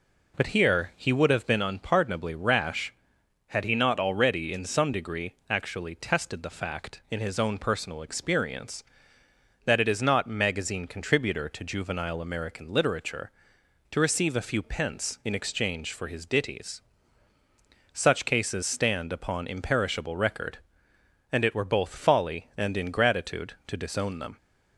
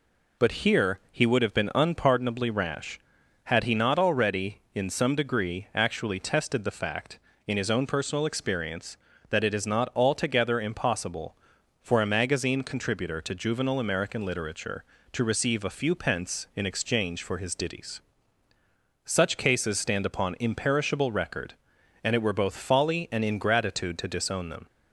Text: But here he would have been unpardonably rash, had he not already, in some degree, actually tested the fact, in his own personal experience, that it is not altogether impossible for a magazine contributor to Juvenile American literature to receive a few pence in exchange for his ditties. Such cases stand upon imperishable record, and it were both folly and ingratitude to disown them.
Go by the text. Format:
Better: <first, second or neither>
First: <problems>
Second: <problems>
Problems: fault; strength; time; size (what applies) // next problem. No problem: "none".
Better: second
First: skips "altogether impossible for a"; at 10.2 s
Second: none